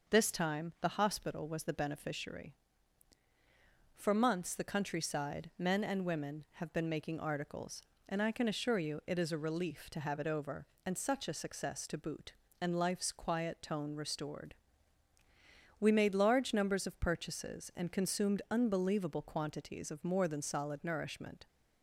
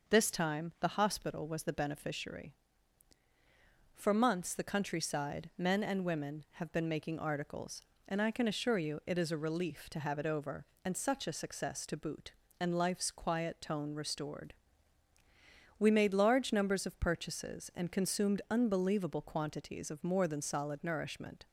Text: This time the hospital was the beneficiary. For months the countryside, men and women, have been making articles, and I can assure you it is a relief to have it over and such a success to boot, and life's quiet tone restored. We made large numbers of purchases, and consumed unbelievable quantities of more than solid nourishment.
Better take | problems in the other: neither | none

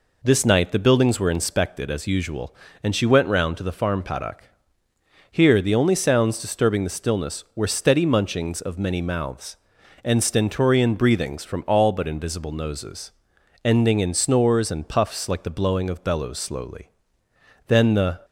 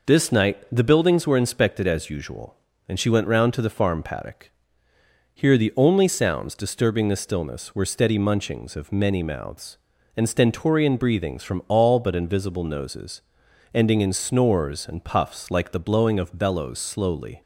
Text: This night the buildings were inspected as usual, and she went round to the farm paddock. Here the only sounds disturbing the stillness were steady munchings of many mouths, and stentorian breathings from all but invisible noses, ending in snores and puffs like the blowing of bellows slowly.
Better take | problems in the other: second | goes on to say "Then the"; from 17.6 s on; 0.54 s long

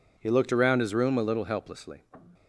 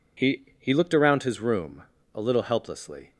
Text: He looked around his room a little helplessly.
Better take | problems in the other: first | says "He" twice; at 0.5 s // pauses between "room" and "a"; slight; at 1.8 s; 0.28 s long

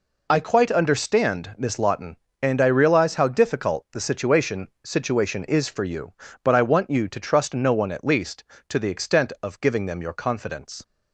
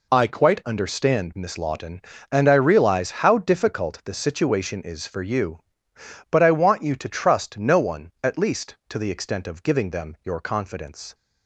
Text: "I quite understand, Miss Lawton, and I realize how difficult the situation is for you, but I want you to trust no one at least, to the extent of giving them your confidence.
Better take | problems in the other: second | says "situation" twice; at 4.8 s

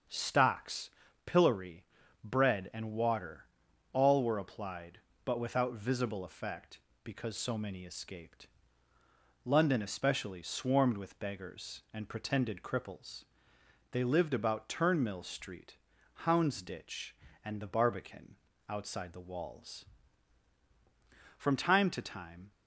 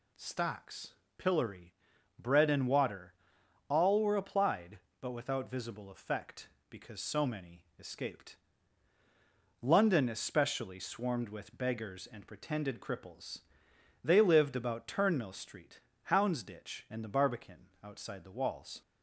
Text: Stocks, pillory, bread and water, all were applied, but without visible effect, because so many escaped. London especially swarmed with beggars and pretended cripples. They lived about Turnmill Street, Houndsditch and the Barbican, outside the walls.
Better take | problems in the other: second | starts louder than the rest; until 1.4 s; 7 dB // goes on to say "From time to time"; noticeable; from 21.3 s on; 1.1 s long

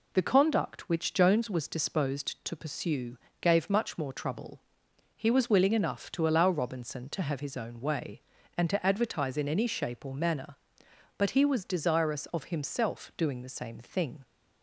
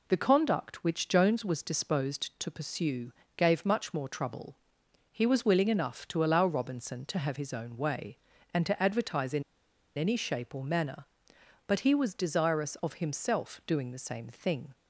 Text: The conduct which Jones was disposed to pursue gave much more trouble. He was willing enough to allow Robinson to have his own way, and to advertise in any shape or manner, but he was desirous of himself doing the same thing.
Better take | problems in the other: first | pauses between "pursue" and "gave"; slight; at 3.1 s; 0.24 s long; slight in the first // pauses between "in" and "any"; noticeable; at 9.4 s; 0.54 s long

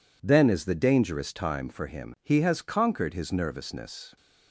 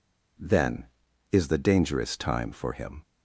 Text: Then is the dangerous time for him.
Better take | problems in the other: second | goes on to say "He has conquered his nervousness"; strong; from 2.2 s on; 1.9 s long

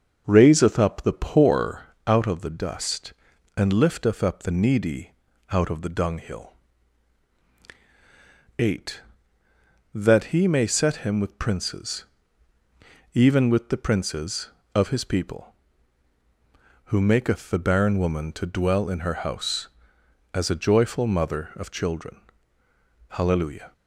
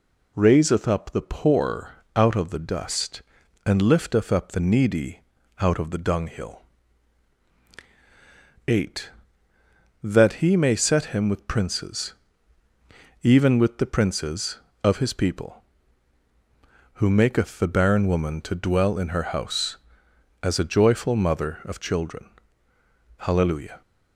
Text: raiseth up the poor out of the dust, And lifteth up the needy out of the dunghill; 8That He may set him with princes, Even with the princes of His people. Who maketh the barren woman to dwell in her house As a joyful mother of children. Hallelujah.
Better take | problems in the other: second | starts louder than the rest; until 1.9 s; 6 dB // pauses between "poor" and "out"; slight; at 1.8 s; 0.24 s long; slight in the second // pauses between "needy" and "out"; at 5.1 s; 0.40 s long; also in the second

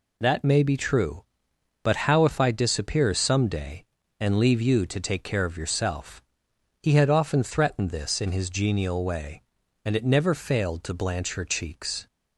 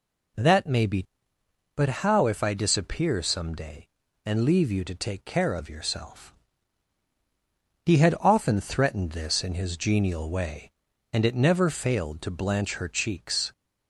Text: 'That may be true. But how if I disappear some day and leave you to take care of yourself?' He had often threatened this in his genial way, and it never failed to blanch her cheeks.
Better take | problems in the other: first | skips "true"; at 1.3 s

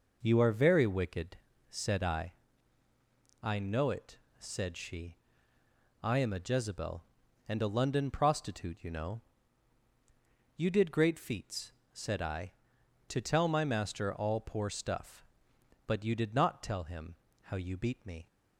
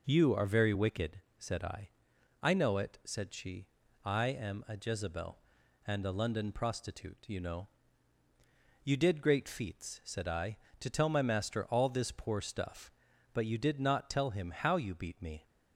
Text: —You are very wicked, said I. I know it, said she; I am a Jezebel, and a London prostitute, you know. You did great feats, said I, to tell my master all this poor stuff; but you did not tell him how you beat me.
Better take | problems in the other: second | skips "this"; at 14.4 s // pauses between "him" and "how"; slight; at 17.1 s; 0.30 s long

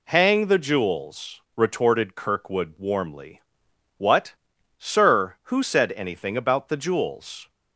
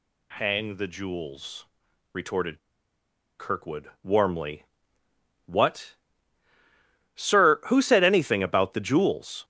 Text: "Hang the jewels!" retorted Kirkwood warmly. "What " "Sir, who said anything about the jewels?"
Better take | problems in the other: first | pauses between "retorted" and "Kirkwood"; noticeable; at 2.5 s; 0.81 s long

